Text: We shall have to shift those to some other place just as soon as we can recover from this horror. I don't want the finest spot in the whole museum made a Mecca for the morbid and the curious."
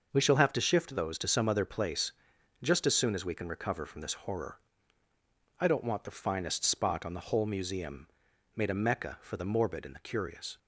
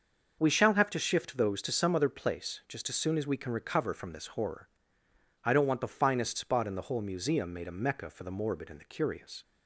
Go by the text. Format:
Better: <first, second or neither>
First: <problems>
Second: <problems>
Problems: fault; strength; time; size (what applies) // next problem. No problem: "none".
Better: second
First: starts louder than the rest; noticeable; until 1.1 s; 6 dB // pauses between "place" and "just"; noticeable; at 2.1 s; 0.50 s long // says "on" for "in"; at 7.0 s // pauses between "museum" and "made"; noticeable; at 8.0 s; 0.48 s long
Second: starts louder than the rest; until 1.4 s; 6 dB